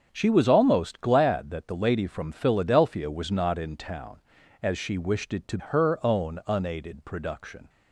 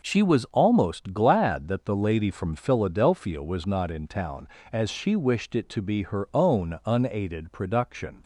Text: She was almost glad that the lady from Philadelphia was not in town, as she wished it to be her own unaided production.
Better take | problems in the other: second | starts louder than the rest; until 1.1 s; 7 dB // skips "be"; at 5.5 s

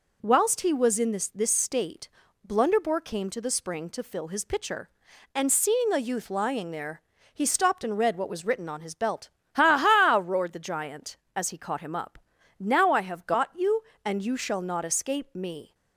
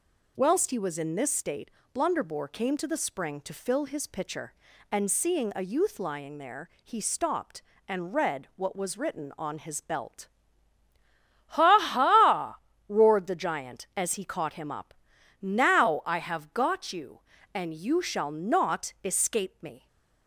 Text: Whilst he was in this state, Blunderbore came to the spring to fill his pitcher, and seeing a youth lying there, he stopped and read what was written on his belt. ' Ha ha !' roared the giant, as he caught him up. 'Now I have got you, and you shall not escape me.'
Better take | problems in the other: second | says "this" twice; at 1.2 s

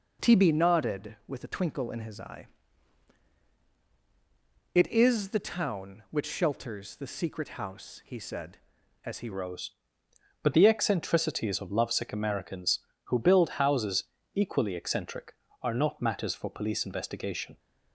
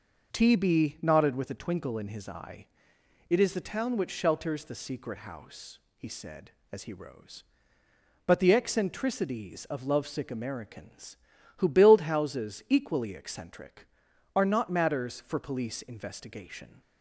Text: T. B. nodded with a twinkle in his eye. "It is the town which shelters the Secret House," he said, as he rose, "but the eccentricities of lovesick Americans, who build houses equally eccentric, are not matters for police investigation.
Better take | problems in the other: second | changes voice at "rose"; from 9.3 s on; 8.2 s long // pauses between "houses" and "equally"; slight; at 14.0 s; 0.32 s long

